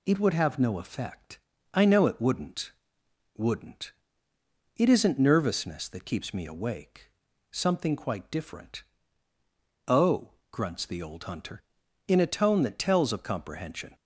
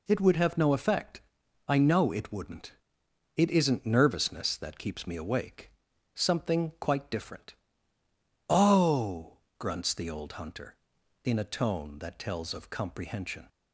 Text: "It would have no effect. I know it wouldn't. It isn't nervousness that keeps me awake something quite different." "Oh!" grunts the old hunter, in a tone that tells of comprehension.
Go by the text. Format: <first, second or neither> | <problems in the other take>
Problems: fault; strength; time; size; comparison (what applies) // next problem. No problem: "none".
second | says "wouldn't" twice; at 3.3 s // pauses between "awake" and "something"; at 7.0 s; 0.42 s long; also in the second